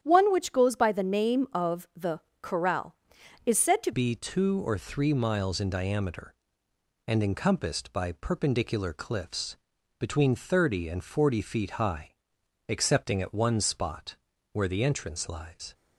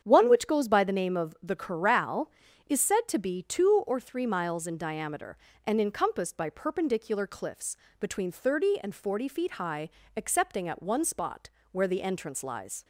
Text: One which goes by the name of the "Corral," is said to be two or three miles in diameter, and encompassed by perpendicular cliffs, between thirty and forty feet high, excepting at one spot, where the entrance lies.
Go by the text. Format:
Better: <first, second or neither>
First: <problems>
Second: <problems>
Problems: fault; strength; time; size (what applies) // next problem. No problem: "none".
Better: second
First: starts louder than the rest; strong; until 1.0 s; 9.5 dB // pauses between "the" and "Corral"; slight; at 2.2 s; 0.20 s long // changes voice at "be"; from 3.9 s on; 11.8 s long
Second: starts louder than the rest; strong; until 1.0 s; 8 dB